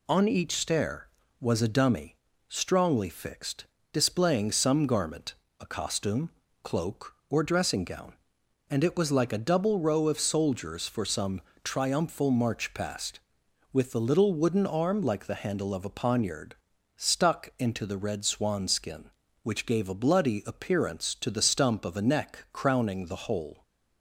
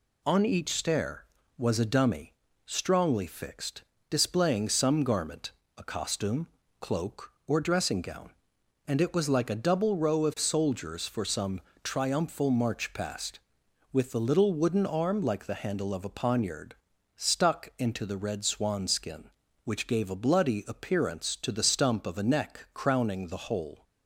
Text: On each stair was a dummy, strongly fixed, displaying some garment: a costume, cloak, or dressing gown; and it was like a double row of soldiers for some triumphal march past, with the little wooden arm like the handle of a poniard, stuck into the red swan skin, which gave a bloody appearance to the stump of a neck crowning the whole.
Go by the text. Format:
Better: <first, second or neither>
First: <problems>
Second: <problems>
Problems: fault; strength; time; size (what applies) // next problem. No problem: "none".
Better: neither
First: pauses between "some" and "triumphal"; slight; at 11.4 s; 0.22 s long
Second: pauses between "some" and "triumphal"; slight; at 11.6 s; 0.22 s long